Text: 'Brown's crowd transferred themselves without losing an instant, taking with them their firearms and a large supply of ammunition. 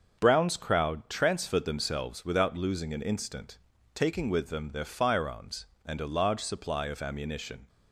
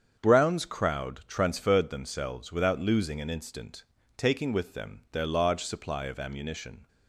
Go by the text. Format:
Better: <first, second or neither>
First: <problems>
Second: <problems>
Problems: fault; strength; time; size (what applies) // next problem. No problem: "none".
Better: first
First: starts louder than the rest; until 1.2 s; 6.5 dB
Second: starts louder than the rest; strong; until 1.2 s; 7.5 dB // skips "firearms and a"; at 5.2 s